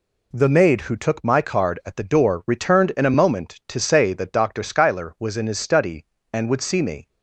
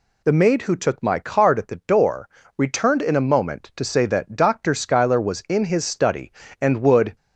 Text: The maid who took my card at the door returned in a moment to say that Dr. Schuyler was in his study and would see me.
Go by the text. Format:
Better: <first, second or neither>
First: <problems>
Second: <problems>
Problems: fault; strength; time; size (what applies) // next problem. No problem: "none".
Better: first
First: none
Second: pauses between "door" and "returned"; slight; at 2.2 s; 0.30 s long // stops before "see me"; at 7.1 s